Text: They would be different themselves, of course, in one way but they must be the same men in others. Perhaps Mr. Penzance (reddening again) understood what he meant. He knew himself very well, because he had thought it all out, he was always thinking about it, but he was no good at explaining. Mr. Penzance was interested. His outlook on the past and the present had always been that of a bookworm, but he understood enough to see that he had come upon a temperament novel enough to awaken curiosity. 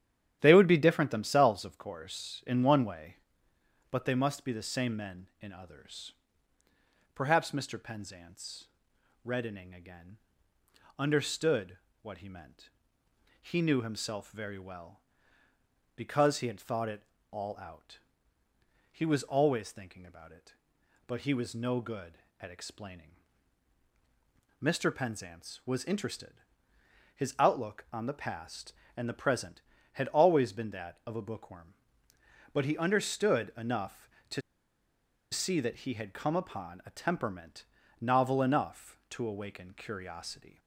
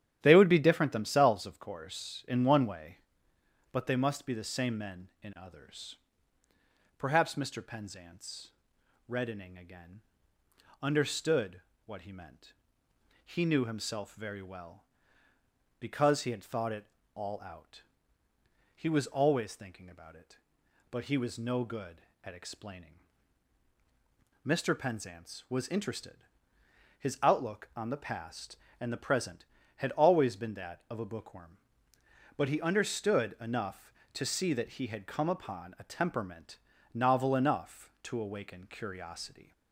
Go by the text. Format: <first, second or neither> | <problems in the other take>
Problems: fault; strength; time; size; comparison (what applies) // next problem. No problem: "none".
second | starts louder than the rest; strong; until 1.4 s; 10.5 dB; strong in the second // pauses between "understood" and "what"; slight; at 11.7 s; 0.26 s long; slight in the second // pauses between "it" and "all"; slight; at 17.0 s; 0.30 s long; slight in the second // pauses between "to" and "see"; noticeable; at 34.4 s; 0.91 s long // pauses between "temperament" and "novel"; slight; at 37.6 s; 0.36 s long; slight in the second